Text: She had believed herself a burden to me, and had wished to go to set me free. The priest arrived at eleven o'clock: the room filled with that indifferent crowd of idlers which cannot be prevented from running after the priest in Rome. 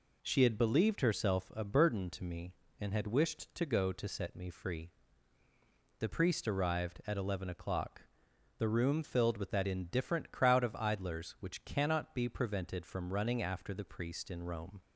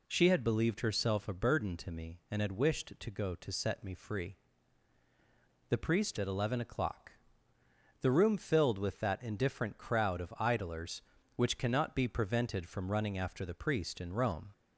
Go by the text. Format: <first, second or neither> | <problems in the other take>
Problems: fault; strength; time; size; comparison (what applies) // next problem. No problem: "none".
first | skips "arrived"; at 6.1 s